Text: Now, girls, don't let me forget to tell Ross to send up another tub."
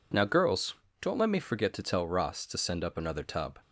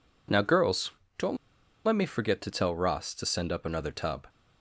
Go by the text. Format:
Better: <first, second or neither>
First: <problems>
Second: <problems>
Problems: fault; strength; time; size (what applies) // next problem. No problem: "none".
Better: first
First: none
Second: pauses between "don't" and "let"; noticeable; at 1.3 s; 0.50 s long